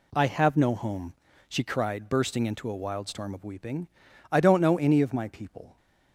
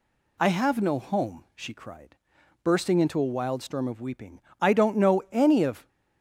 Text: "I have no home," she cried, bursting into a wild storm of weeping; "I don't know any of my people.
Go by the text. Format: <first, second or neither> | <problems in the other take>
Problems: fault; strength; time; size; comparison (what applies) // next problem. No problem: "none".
first | stops before "my people"; at 5.8 s